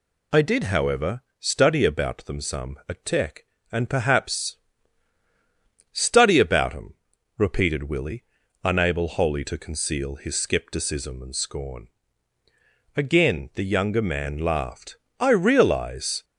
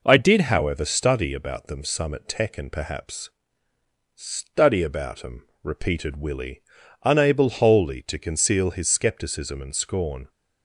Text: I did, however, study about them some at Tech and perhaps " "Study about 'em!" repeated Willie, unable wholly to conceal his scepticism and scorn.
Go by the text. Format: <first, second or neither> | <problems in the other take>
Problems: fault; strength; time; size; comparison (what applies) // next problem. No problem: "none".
second | goes on to say "Again the younger man laughed I realize"; strong; from 12.9 s on; 3.2 s long